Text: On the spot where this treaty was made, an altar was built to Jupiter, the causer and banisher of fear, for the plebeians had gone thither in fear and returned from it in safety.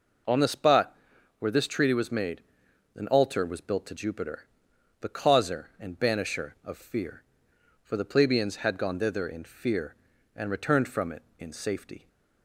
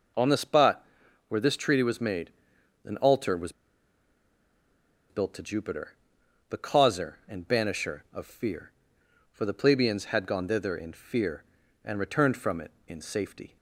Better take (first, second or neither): first